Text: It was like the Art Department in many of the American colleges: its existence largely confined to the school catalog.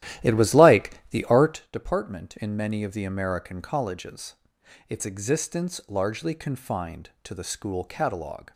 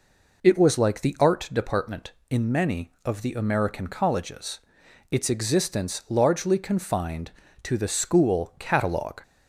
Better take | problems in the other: second | starts louder than the rest; strong; until 1.7 s; 13 dB

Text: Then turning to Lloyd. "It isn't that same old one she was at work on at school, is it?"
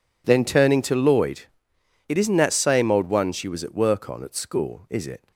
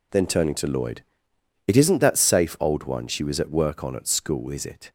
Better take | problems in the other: first | says "safe" for "same"; at 2.1 s

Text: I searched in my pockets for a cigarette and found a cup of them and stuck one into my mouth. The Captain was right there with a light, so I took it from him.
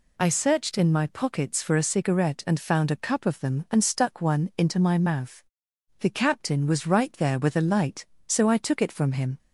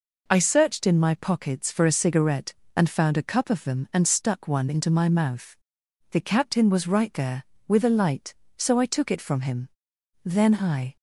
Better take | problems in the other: first | goes on to say "Then I"; noticeable; from 10.2 s on; 0.72 s long

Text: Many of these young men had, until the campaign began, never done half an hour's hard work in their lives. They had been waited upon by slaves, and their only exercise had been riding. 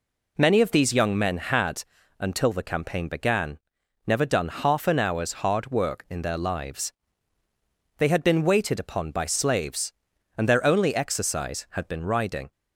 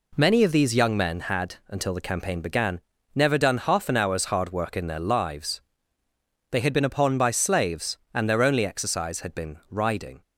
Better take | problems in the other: first | skips "waited"; at 6.8 s

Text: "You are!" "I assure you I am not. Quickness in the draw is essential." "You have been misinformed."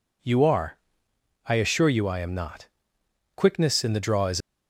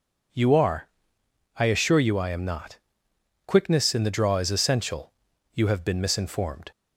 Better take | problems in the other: second | stops before "essential You have been misinformed"; at 4.4 s

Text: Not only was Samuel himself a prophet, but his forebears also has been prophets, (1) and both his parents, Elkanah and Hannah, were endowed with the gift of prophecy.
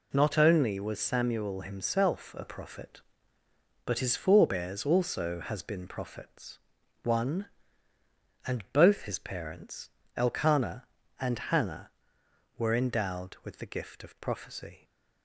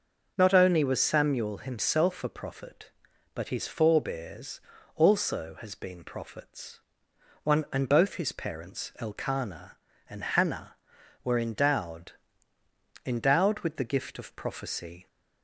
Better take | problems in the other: first | pauses between "forebears" and "also"; slight; at 4.6 s; 0.34 s long // says "endowed" twice; at 13.0 s

